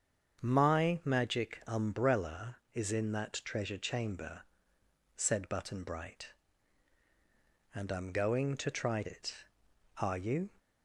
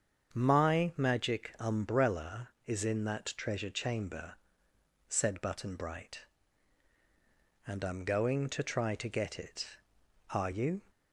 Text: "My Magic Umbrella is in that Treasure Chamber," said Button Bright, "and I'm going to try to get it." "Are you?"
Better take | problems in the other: second | starts louder than the rest; strong; until 1.4 s; 7 dB; strong in the second // skips "to get"; at 9.0 s

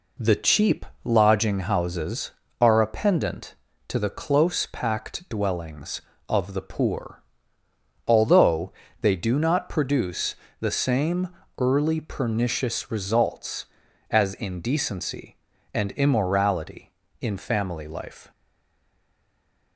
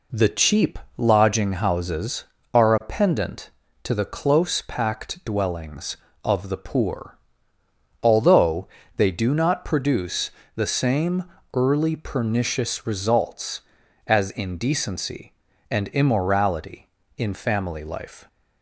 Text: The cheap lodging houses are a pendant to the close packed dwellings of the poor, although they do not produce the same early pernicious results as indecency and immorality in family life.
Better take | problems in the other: second | pauses between "cheap" and "lodging"; slight; at 0.8 s; 0.20 s long; slight in the second // pauses between "although" and "they"; slight; at 8.7 s; 0.28 s long; slight in the second // pauses between "produce" and "the"; slight; at 10.3 s; 0.24 s long; slight in the second // pauses between "same" and "early"; slight; at 11.2 s; 0.32 s long; slight in the second // stays silent after the last word; noticeable; from 18.3 s on; 1.4 s long

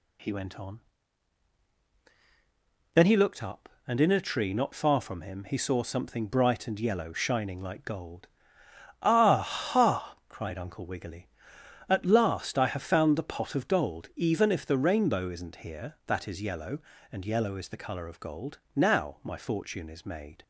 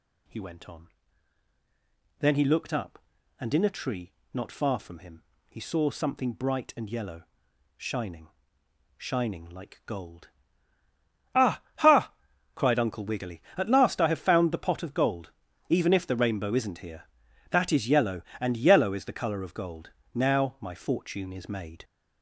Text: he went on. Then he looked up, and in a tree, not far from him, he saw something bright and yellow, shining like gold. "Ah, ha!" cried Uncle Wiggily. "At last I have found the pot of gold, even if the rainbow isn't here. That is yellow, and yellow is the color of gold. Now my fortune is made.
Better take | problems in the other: first | says "shining" twice; at 8.9 s

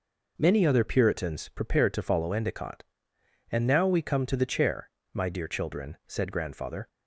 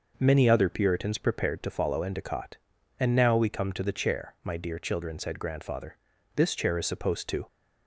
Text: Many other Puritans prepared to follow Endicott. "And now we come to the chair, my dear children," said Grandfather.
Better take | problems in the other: first | goes on to say "This chair is supposed to"; noticeable; from 6.3 s on; 1.1 s long

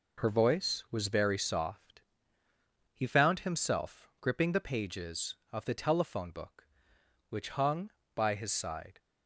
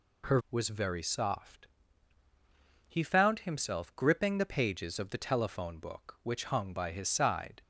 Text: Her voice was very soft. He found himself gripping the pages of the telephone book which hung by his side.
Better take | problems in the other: first | skips "voice"; at 0.4 s

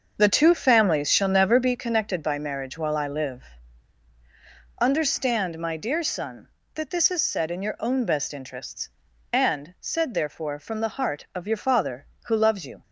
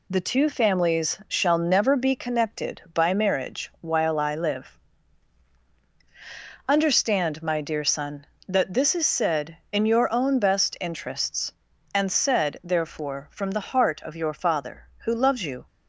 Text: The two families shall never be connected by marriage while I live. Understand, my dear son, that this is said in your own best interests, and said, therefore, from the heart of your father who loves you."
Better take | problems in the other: second | starts louder than the rest; until 1.8 s; 6.5 dB

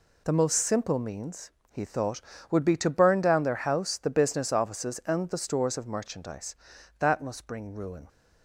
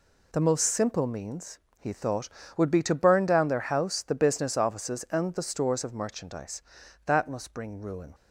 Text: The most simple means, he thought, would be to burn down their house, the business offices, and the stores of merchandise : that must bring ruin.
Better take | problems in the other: neither | none

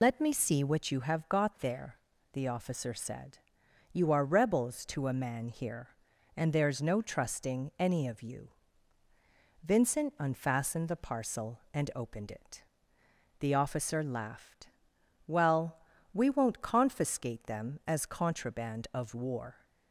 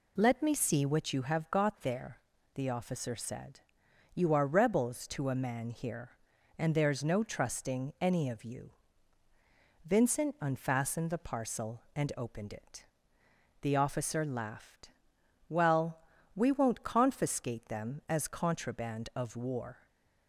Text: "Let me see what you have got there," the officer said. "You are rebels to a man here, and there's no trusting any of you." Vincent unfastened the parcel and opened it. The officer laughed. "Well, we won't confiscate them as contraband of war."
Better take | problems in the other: second | loses the start of "Let"; at 0.0 s; 75 ms

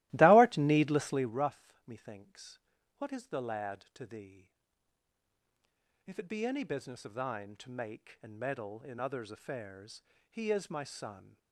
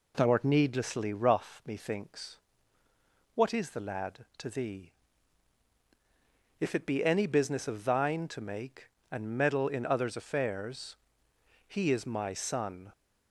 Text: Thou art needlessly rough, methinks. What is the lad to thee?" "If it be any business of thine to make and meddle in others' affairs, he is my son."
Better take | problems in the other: second | starts louder than the rest; strong; until 1.4 s; 17 dB

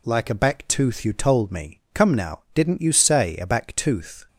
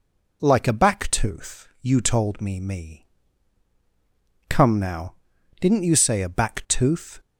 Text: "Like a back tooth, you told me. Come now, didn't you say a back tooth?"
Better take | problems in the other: first | says "me" twice; at 2.5 s

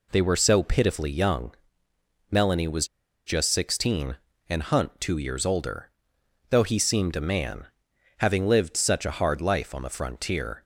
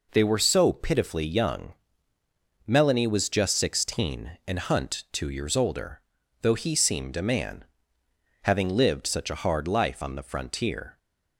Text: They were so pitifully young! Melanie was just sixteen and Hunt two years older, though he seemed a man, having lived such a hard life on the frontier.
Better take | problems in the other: second | pauses between "was" and "just"; at 2.8 s; 0.39 s long

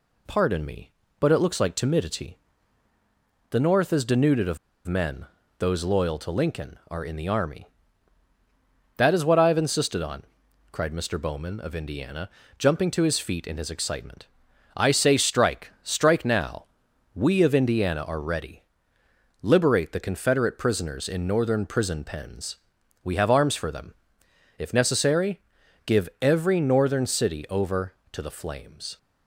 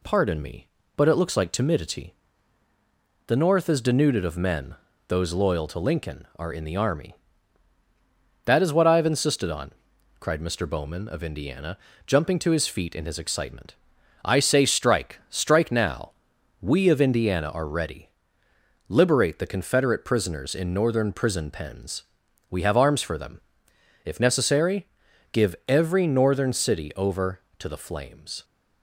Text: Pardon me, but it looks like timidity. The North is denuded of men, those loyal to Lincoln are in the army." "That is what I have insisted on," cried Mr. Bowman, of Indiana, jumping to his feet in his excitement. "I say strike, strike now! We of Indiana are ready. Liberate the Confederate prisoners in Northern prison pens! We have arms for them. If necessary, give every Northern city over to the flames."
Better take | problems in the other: second | pauses between "of" and "men"; slight; at 4.5 s; 0.29 s long

